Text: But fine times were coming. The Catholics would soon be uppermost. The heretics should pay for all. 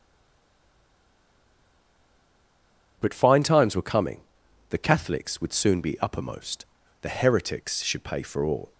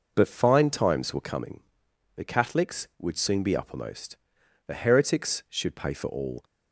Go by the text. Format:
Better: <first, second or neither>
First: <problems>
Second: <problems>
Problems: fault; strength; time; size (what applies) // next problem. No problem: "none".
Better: second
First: stays silent before the first word; strong; until 2.9 s; 2.9 s long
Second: none